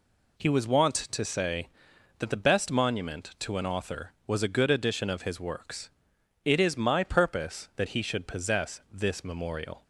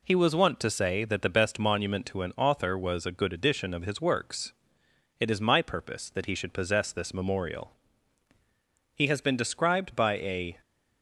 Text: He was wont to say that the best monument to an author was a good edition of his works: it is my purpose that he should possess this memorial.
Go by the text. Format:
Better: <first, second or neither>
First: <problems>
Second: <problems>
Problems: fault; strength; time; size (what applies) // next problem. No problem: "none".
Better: first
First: none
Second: goes on to say "He has been described by a"; from 8.9 s on; 1.6 s long